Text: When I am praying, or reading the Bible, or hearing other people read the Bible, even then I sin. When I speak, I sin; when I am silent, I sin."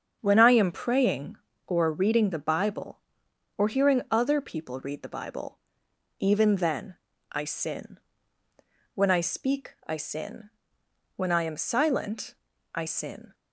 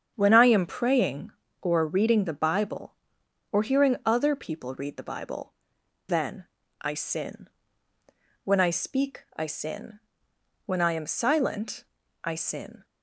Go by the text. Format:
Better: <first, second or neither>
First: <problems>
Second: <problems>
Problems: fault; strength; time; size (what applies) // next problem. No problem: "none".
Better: first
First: starts louder than the rest; strong; until 1.2 s; 7.5 dB // pauses between "then" and "I"; slight; at 6.9 s; 0.36 s long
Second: starts louder than the rest; strong; until 1.1 s; 7.5 dB // skips "even"; at 5.8 s // pauses between "then" and "I"; slight; at 6.4 s; 0.36 s long